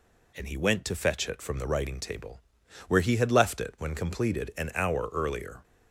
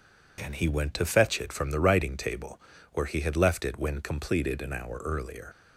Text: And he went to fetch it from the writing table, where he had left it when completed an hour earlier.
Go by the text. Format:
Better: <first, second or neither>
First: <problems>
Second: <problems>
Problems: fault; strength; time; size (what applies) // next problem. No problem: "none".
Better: first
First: none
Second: leaves "earlier" unfinished; at 5.5 s; 75 ms